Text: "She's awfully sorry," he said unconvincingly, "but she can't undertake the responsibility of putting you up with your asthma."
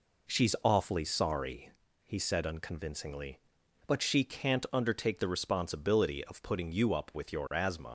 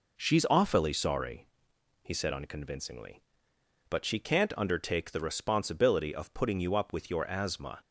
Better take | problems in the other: second | leaves "asthma" unfinished; at 7.8 s; 115 ms

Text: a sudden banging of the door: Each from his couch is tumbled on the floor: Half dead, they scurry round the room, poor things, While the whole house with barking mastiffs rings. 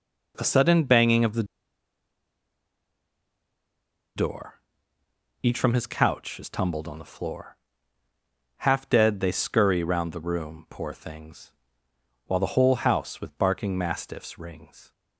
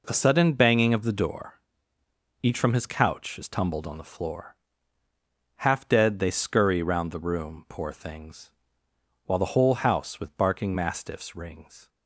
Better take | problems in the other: second | pauses between "the" and "door"; strong; at 1.4 s; 2.7 s long

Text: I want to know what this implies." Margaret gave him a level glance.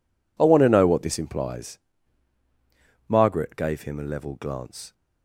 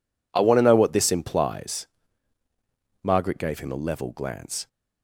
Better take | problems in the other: neither | none

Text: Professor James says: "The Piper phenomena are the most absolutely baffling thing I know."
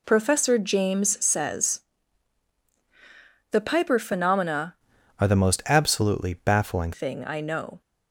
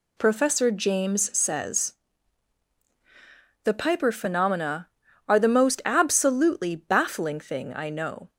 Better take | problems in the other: second | changes voice from "are" to "baffling"; from 5.1 to 6.9 s; 1.8 s long

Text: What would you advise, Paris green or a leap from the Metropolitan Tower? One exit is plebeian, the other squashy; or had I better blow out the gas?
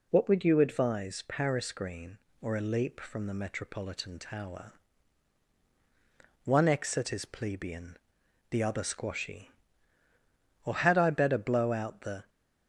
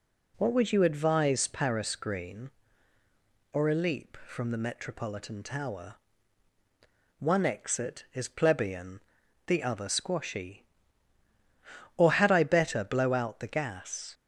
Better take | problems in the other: second | stops before "gas"; at 12.2 s

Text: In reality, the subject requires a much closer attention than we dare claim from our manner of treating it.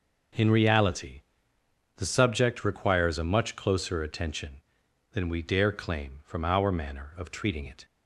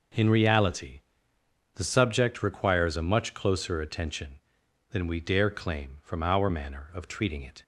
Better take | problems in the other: neither | none

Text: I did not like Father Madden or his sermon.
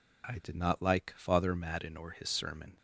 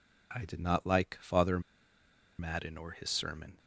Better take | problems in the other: first | pauses between "Father" and "Madden"; noticeable; at 1.5 s; 0.79 s long

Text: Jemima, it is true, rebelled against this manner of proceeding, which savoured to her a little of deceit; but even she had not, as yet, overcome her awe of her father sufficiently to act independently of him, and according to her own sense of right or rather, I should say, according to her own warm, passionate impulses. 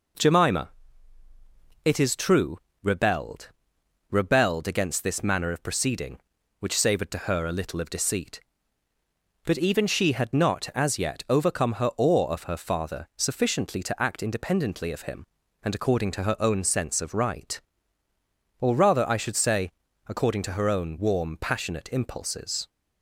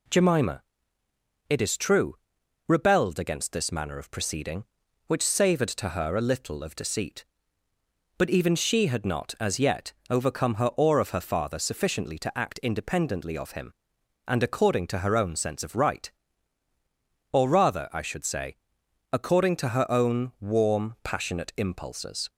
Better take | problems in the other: second | says "rebelled" twice; at 4.1 s

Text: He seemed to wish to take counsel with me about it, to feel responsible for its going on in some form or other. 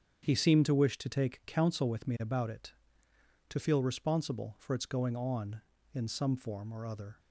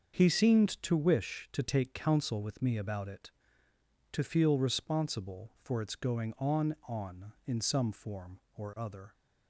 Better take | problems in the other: first | starts louder than the rest; until 1.1 s; 6.5 dB; strong in the first // says "on" twice; at 6.8 s

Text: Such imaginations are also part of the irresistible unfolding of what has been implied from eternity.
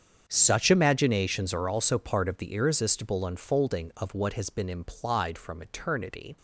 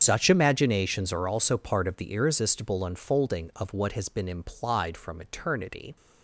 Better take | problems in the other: first | loses the start of "Such"; at 0.0 s; 135 ms // starts louder than the rest; strong; until 1.0 s; 7.5 dB; strong in the first

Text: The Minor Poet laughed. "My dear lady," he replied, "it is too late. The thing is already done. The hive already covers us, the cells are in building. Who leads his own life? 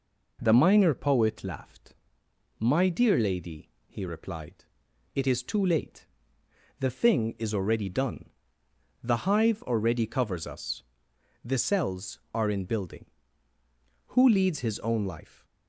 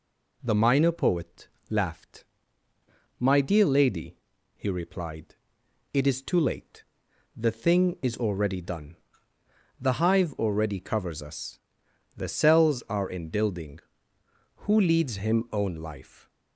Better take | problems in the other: first | pauses between "Poet" and "laughed"; slight; at 1.4 s; 0.20 s long // says "him" for "his"; at 15.1 s

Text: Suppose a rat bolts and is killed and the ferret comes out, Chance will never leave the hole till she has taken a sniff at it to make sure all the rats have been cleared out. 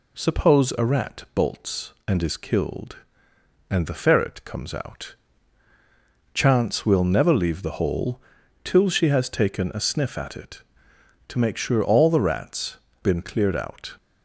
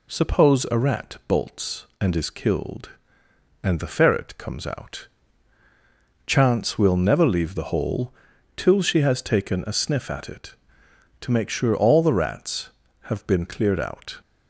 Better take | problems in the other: second | pauses between "hole" and "till"; at 8.2 s; 0.42 s long; also in the second // skips "have"; at 12.8 s

